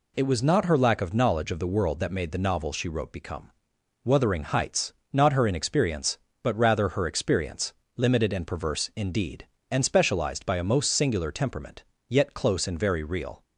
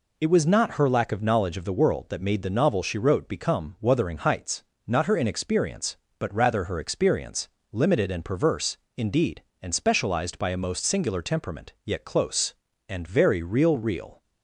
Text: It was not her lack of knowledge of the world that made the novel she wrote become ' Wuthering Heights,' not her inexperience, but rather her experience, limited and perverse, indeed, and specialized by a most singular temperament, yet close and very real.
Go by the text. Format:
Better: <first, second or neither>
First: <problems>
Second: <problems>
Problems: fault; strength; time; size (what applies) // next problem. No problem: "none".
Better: first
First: none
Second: says "real" twice; at 13.7 s